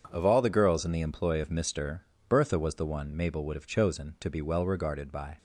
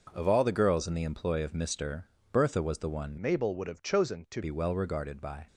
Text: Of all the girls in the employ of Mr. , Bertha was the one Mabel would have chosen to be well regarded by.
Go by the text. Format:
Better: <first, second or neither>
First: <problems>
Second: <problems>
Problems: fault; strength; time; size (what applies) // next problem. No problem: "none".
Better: first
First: none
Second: changes voice from "Mabel" to "to"; from 3.2 to 4.4 s; 1.2 s long